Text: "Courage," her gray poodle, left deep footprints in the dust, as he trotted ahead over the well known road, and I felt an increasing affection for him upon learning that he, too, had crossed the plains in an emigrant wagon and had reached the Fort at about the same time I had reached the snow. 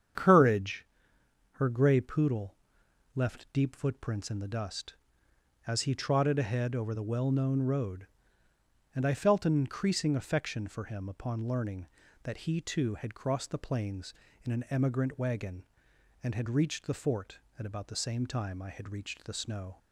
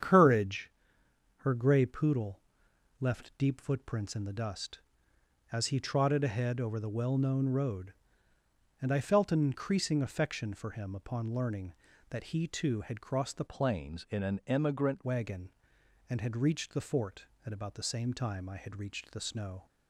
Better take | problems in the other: first | starts louder than the rest; strong; until 1.7 s; 8 dB; strong in the first // changes voice from "plains" to "emigrant"; from 13.4 to 15.0 s; 1.6 s long

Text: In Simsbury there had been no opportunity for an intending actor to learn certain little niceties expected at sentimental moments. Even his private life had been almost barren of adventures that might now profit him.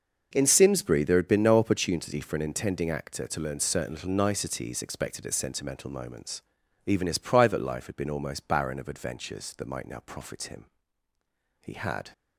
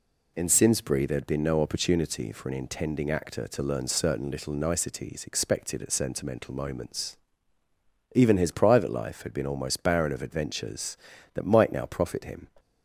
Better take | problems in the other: second | goes on to say "He had"; from 11.6 s on; 0.52 s long

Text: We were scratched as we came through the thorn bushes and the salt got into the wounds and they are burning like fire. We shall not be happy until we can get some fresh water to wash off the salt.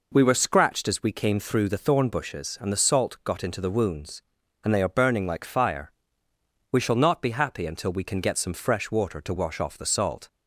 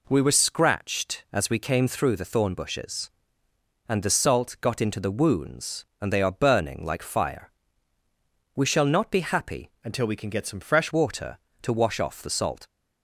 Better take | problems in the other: first | changes voice from "until" to "fresh"; from 9.8 to 10.9 s; 1.1 s long

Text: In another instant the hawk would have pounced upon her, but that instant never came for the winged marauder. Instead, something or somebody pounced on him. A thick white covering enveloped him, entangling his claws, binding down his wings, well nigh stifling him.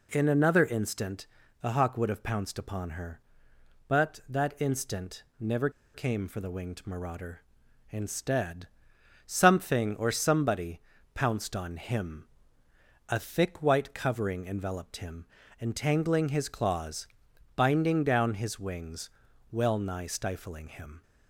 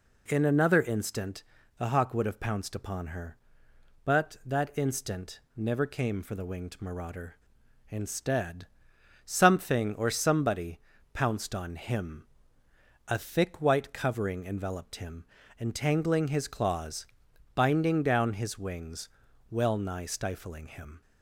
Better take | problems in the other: second | pauses between "instant" and "the"; slight; at 1.2 s; 0.34 s long; slight in the second // pauses between "instant" and "never"; slight; at 5.2 s; 0.16 s long; slight in the second // pauses between "never" and "came"; slight; at 5.6 s; 0.24 s long // pauses between "somebody" and "pounced"; slight; at 10.7 s; 0.34 s long; slight in the second

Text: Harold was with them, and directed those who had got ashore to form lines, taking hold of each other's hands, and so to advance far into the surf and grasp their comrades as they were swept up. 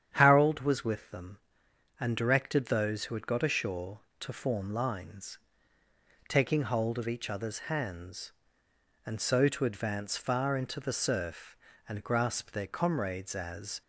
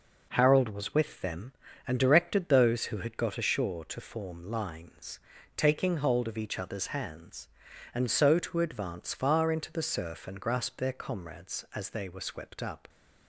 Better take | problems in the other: second | starts louder than the rest; strong; until 1.1 s; 9 dB // stops before "they were swept up"; at 13.8 s

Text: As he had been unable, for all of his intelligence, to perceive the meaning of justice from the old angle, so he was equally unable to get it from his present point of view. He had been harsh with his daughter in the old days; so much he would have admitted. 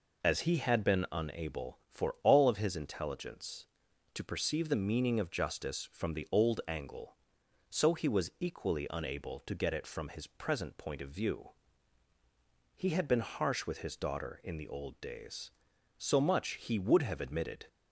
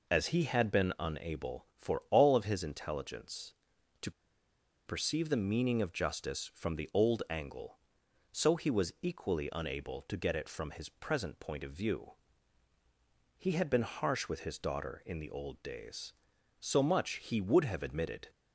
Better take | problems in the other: first | pauses between "to" and "perceive"; noticeable; at 4.1 s; 0.75 s long

